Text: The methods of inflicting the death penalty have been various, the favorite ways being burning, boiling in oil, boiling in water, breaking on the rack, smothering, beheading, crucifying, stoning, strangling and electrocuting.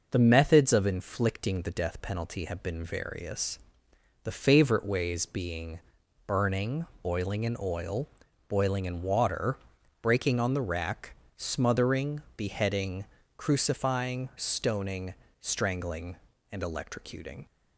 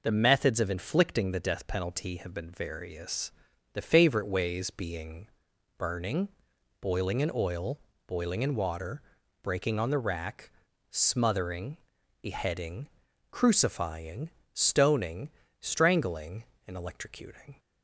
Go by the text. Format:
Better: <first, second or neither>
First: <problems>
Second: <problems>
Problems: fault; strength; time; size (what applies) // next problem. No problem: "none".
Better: neither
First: pauses between "being" and "burning"; noticeable; at 5.7 s; 0.48 s long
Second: pauses between "being" and "burning"; noticeable; at 5.2 s; 0.50 s long